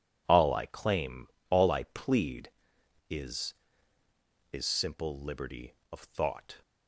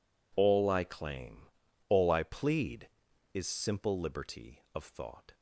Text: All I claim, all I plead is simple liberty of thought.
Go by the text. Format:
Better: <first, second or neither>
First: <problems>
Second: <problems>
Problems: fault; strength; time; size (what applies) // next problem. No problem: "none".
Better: second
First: says "is" twice; at 4.5 s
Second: none